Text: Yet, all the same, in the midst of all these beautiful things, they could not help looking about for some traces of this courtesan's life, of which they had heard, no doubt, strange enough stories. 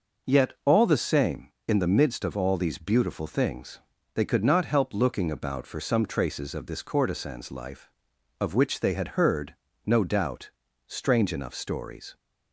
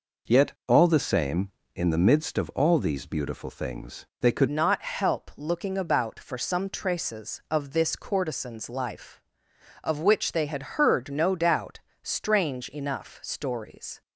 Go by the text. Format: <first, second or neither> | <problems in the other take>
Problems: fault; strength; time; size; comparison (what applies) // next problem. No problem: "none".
first | changes voice at "not"; from 4.4 s on; 9.6 s long